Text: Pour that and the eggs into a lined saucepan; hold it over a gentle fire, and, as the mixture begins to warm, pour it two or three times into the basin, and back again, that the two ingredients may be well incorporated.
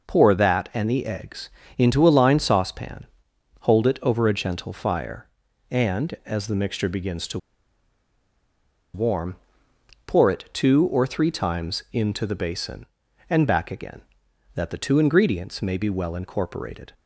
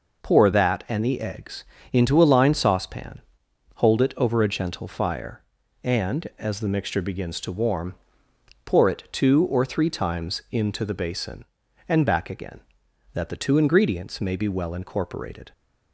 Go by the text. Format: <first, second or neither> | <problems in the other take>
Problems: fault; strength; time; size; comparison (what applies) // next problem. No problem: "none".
second | pauses between "eggs" and "into"; slight; at 1.4 s; 0.28 s long; slight in the second // pauses between "to" and "warm"; strong; at 7.3 s; 1.5 s long